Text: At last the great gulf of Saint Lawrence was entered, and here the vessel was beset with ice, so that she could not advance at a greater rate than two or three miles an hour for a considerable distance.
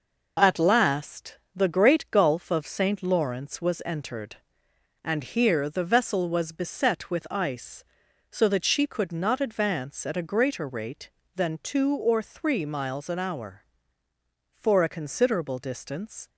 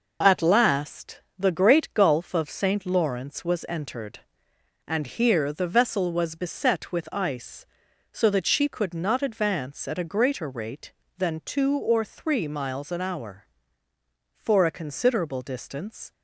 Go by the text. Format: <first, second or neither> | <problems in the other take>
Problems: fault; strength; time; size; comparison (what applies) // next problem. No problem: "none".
neither | pauses between "last" and "the"; slight; the same in both